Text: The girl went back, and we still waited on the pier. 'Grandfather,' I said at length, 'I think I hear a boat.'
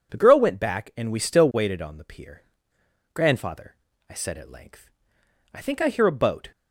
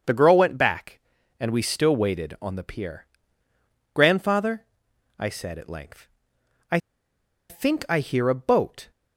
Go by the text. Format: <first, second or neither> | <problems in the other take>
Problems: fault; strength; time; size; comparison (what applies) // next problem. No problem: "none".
first | starts louder than the rest; until 1.4 s; 7 dB // pauses between "I" and "think"; noticeable; at 6.7 s; 0.70 s long